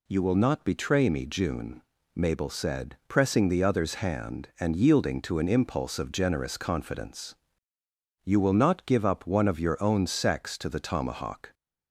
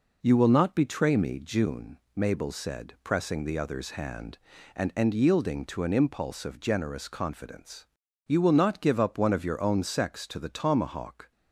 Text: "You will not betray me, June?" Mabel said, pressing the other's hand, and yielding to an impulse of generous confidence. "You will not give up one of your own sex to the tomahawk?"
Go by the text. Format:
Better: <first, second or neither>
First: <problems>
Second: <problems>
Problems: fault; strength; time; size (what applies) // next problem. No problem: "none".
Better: first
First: none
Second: says "and" twice; at 4.9 s